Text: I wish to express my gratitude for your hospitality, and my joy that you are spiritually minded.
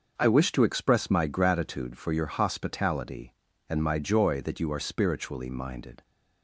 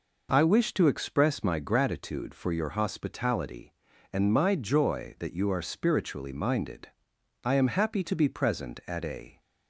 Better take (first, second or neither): first